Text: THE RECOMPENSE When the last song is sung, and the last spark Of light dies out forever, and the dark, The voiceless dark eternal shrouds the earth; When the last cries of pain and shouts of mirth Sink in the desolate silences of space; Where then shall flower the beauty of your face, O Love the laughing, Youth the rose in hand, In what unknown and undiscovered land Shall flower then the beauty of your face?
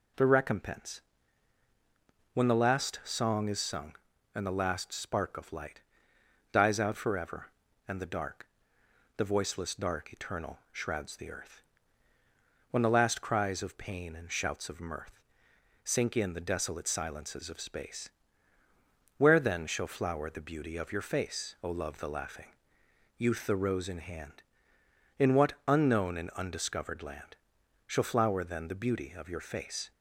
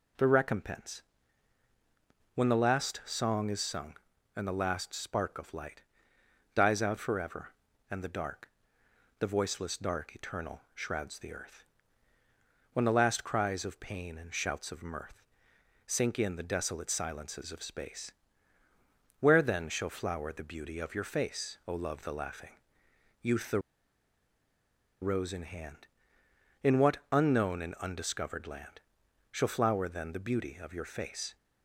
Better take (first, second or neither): first